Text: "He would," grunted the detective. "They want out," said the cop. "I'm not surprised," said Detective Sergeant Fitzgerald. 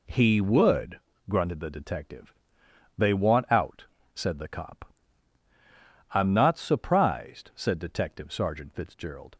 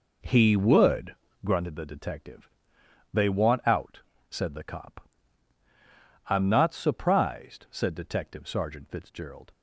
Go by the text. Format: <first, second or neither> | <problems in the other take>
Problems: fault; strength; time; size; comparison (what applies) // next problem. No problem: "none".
first | starts louder than the rest; noticeable; until 1.6 s; 4.5 dB